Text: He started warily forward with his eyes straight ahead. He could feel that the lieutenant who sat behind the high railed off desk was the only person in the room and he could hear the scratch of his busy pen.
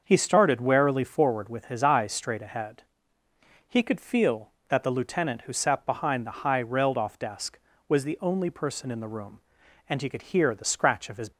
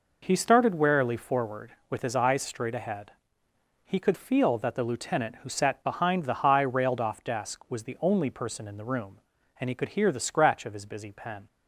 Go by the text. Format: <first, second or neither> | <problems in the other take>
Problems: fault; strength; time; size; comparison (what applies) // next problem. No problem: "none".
second | starts louder than the rest; until 1.0 s; 6.5 dB // stops before "busy pen"; at 11.3 s